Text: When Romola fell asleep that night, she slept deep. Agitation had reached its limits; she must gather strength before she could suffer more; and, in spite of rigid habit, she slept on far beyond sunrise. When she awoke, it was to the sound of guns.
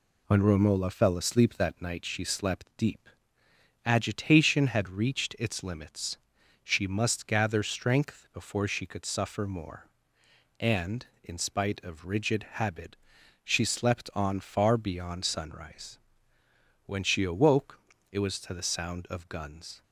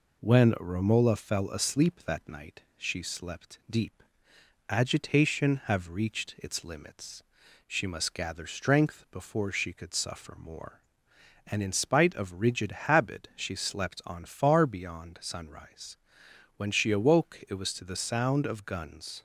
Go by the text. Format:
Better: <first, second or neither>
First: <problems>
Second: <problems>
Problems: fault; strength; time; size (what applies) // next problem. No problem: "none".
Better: first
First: none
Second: says "have" for "had"; at 5.6 s